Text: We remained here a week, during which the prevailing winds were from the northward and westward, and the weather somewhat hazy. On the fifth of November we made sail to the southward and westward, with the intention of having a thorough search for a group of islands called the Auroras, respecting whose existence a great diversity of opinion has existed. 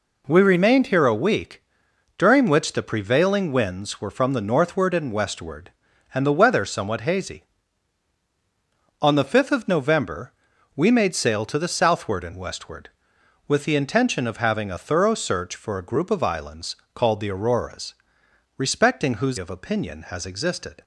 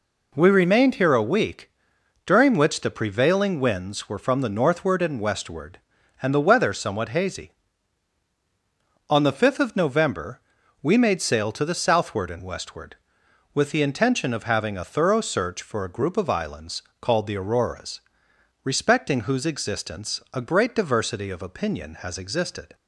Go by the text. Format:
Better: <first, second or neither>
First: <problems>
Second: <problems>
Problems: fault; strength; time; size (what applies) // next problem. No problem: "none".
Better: second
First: pauses between "November" and "we"; at 10.3 s; 0.44 s long // pauses between "islands" and "called"; slight; at 16.7 s; 0.18 s long // skips "existence a great diversity"; at 19.3 s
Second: pauses between "November" and "we"; at 10.4 s; 0.42 s long // pauses between "islands" and "called"; slight; at 16.8 s; 0.18 s long